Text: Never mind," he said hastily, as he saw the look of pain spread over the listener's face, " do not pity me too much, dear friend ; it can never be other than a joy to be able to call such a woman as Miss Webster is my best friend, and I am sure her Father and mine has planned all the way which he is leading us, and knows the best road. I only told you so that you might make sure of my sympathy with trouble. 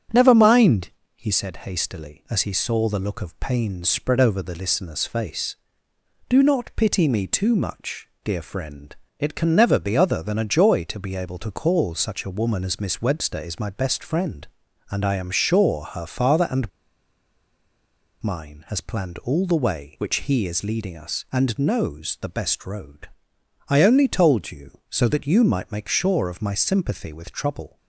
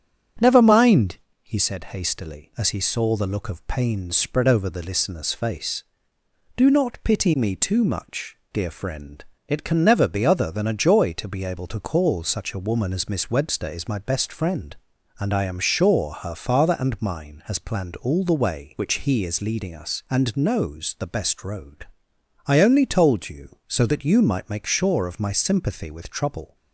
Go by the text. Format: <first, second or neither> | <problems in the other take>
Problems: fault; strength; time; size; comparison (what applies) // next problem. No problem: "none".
second | starts louder than the rest; strong; until 1.3 s; 9 dB; strong in the second // pauses between "and" and "mine"; strong; at 16.7 s; 1.5 s long